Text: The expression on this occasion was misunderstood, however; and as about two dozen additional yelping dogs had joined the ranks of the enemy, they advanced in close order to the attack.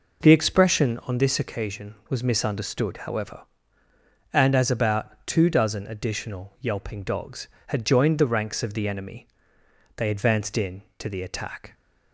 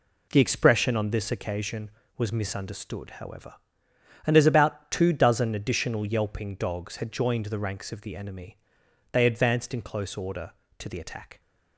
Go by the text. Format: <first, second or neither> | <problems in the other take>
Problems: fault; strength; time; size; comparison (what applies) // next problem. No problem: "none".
second | skips "close order"; at 10.9 s